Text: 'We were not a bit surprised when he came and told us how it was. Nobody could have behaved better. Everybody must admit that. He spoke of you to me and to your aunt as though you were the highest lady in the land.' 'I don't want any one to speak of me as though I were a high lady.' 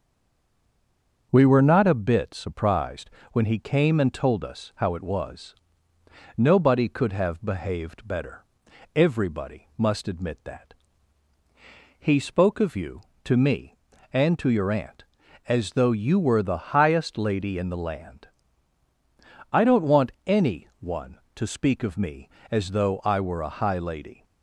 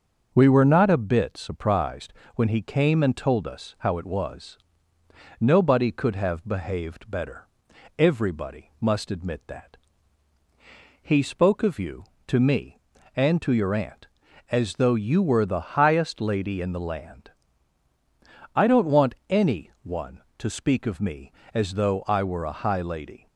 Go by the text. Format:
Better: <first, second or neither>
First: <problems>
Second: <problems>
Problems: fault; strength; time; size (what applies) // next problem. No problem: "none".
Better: second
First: stays silent before the first word; noticeable; until 1.3 s; 1.3 s long // starts louder than the rest; until 2.3 s; 6.5 dB // pauses between "surprised" and "when"; slight; at 3.0 s; 0.24 s long // pauses between "want" and "any"; slight; at 20.1 s; 0.16 s long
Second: starts louder than the rest; until 1.3 s; 6.5 dB // pauses between "surprised" and "when"; slight; at 2.1 s; 0.24 s long // pauses between "want" and "any"; slight; at 19.1 s; 0.16 s long